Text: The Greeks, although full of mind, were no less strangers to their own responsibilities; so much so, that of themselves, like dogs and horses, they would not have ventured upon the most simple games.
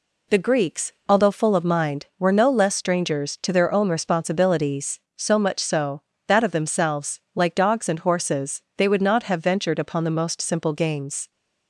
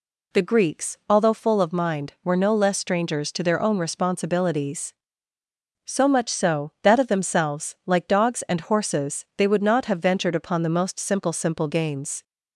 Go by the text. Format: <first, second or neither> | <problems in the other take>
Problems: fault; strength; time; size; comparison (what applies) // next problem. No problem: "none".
first | says "simple" twice; at 11.3 s